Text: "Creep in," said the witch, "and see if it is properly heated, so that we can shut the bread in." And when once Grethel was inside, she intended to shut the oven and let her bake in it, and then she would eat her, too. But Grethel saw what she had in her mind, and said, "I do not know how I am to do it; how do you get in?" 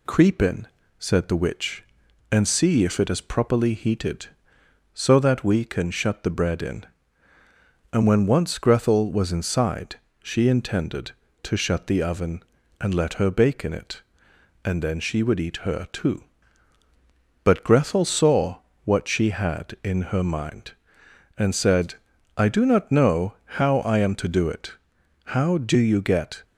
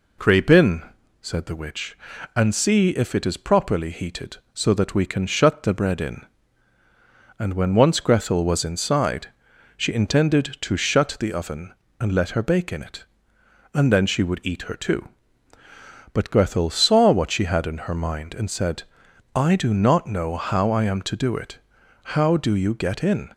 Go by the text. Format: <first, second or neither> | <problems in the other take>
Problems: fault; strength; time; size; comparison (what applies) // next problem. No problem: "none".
second | pauses between "saw" and "what"; slight; at 18.5 s; 0.24 s long // stops before "in"; at 26.4 s